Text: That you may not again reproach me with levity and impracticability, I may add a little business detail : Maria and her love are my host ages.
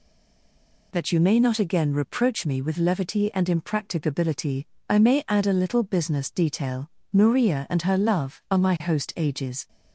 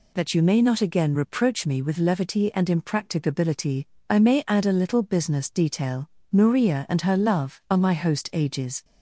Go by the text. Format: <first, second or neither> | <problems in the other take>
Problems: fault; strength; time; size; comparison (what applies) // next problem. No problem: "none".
second | stays silent before the first word; slight; until 0.9 s; 0.9 s long